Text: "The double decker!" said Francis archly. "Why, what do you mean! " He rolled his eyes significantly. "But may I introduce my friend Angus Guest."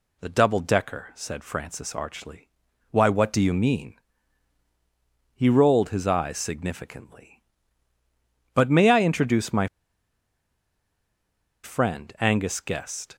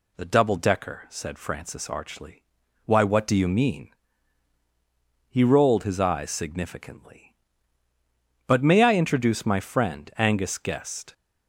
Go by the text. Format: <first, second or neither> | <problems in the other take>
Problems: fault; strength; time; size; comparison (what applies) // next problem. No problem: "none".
second | pauses between "my" and "friend"; strong; at 9.6 s; 1.9 s long